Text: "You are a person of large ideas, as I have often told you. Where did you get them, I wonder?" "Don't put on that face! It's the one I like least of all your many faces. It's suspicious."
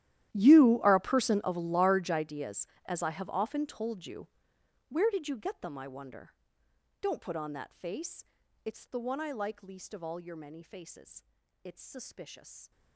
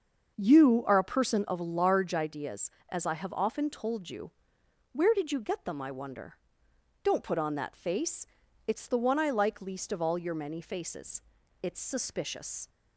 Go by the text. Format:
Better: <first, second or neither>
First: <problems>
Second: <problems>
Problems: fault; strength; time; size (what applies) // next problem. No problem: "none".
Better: second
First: gets quieter; strong; throughout; 21 dB // starts louder than the rest; strong; until 1.3 s; 12.5 dB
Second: starts louder than the rest; until 1.4 s; 6.5 dB